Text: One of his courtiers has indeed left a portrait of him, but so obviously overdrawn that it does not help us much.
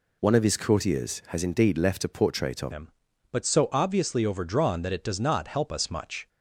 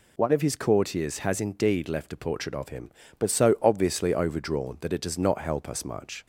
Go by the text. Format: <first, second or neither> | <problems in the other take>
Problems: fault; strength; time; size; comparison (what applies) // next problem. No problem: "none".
second | changes voice at "him"; from 2.7 s on; 3.5 s long